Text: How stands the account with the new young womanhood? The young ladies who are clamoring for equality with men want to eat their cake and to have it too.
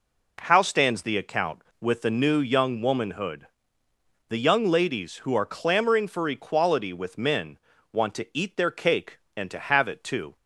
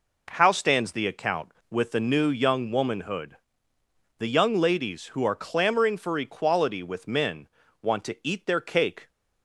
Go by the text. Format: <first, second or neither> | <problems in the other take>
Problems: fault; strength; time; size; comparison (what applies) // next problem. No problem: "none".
first | pauses between "men" and "want"; slight; at 7.4 s; 0.34 s long; slight in the first // stops before "and to have it too"; at 9.0 s